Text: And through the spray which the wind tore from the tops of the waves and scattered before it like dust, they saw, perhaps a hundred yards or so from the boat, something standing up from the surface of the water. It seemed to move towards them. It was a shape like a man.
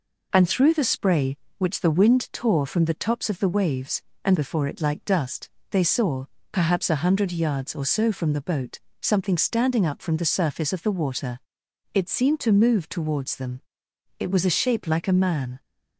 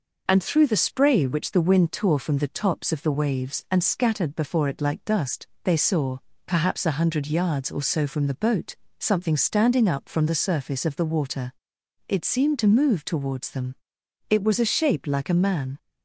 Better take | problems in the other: second | skips "scattered"; at 4.3 s

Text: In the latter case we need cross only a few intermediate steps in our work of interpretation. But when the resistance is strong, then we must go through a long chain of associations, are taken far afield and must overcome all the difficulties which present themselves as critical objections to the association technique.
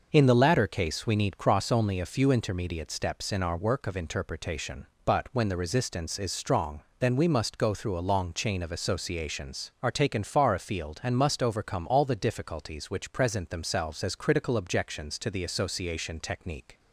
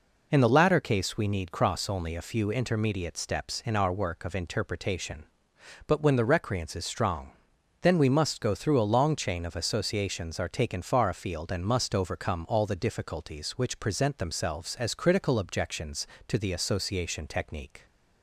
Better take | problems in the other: first | says "recreance" for "resistance"; at 6.2 s

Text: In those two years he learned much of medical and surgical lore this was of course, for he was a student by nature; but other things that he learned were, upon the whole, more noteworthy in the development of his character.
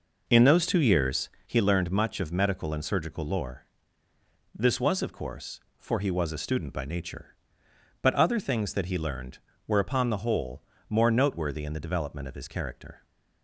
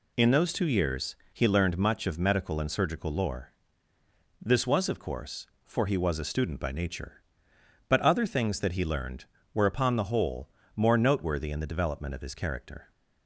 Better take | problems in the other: second | starts louder than the rest; noticeable; until 1.5 s; 5 dB // pauses between "years" and "he"; slight; at 1.2 s; 0.18 s long; slight in the second // pauses between "lore" and "this"; noticeable; at 3.6 s; 0.88 s long; noticeable in the second

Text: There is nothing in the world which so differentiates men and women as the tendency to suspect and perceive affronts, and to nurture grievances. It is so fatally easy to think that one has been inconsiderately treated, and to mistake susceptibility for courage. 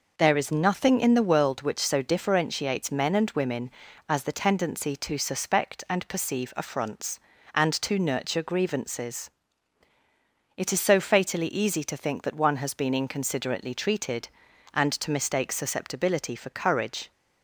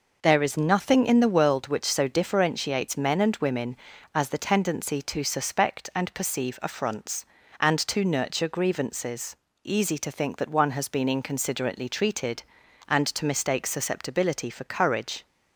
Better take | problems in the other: first | skips "It is so fatally"; at 9.5 s

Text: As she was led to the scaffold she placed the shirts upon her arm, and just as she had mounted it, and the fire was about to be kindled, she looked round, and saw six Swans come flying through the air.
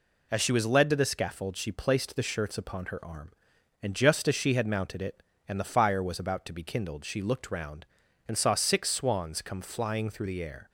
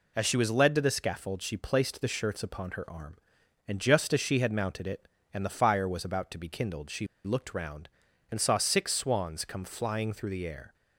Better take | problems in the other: first | pauses between "she" and "looked"; slight; at 7.0 s; 0.19 s long

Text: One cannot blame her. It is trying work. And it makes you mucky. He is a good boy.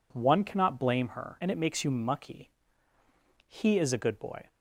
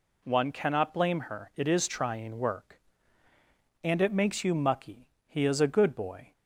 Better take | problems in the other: second | skips "It is trying work"; at 1.3 s

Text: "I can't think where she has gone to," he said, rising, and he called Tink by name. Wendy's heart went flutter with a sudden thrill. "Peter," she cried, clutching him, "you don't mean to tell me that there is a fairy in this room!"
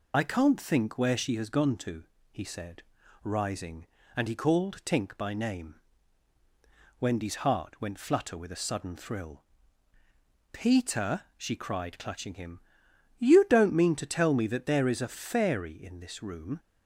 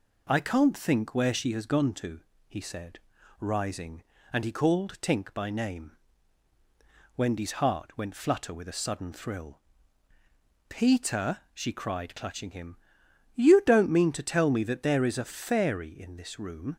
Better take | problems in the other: second | loses the start of "I"; at 0.1 s; 40 ms

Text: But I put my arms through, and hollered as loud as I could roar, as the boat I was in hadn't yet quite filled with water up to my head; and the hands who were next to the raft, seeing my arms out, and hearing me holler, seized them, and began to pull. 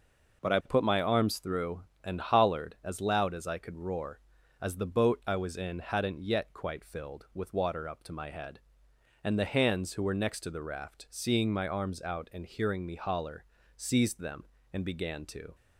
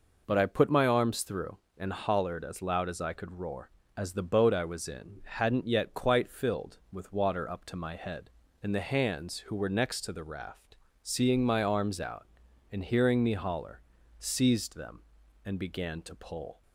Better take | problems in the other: second | stops before "pull"; at 15.5 s

